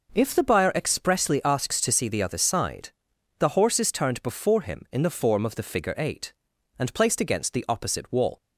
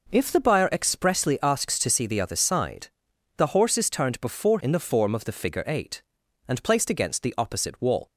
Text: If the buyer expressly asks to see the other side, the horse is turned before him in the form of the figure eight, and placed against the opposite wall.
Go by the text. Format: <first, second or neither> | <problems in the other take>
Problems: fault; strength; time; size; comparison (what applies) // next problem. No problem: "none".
first | skips "him"; at 4.6 s